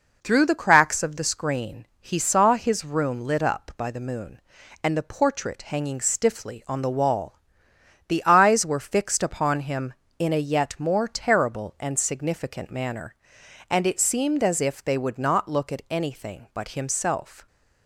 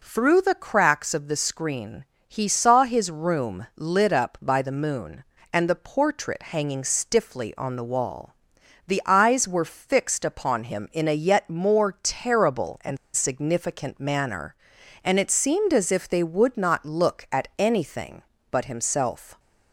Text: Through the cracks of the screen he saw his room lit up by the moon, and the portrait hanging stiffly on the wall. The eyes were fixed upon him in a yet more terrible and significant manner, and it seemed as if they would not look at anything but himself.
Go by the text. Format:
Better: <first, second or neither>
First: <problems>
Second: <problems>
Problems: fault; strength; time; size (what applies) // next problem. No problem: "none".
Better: first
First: none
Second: pauses between "screen" and "he"; slight; at 2.0 s; 0.22 s long // pauses between "and" and "significant"; slight; at 12.9 s; 0.17 s long